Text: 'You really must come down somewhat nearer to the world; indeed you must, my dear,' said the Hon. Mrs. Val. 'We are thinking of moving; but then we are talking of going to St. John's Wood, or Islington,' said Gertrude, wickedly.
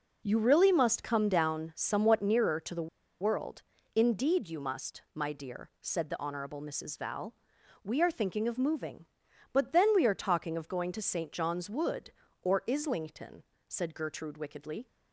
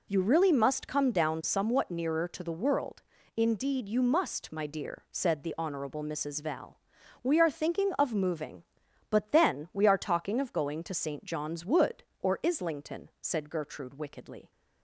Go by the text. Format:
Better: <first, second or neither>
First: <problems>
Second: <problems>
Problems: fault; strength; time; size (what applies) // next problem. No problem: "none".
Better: second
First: pauses between "the" and "world"; slight; at 2.8 s; 0.33 s long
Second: none